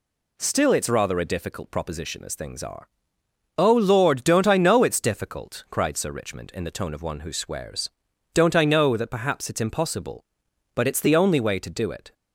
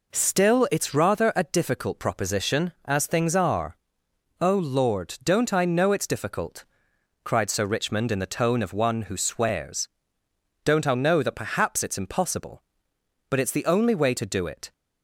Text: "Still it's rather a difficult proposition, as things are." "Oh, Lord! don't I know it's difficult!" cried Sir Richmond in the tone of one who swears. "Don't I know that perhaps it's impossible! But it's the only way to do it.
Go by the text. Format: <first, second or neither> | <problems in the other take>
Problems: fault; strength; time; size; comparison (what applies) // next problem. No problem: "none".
neither | none